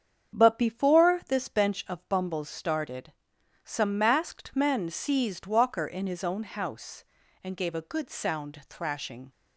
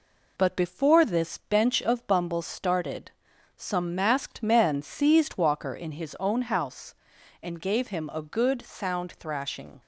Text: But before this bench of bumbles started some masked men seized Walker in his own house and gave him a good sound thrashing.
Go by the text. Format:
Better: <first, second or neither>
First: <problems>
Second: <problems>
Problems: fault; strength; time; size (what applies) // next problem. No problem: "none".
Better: second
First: starts louder than the rest; strong; until 1.4 s; 8 dB // pauses between "started" and "some"; noticeable; at 3.1 s; 0.52 s long // skips "him"; at 7.7 s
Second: pauses between "started" and "some"; noticeable; at 3.1 s; 0.46 s long